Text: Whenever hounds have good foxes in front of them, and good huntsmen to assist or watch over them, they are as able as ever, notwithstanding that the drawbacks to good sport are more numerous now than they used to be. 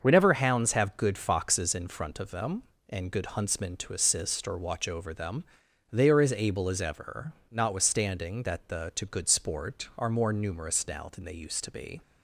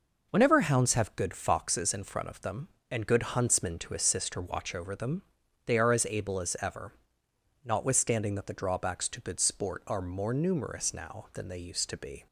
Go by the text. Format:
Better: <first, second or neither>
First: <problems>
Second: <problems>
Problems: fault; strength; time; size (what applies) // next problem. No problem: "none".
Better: second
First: starts louder than the rest; until 1.0 s; 6.5 dB // skips "drawbacks"; at 8.9 s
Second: none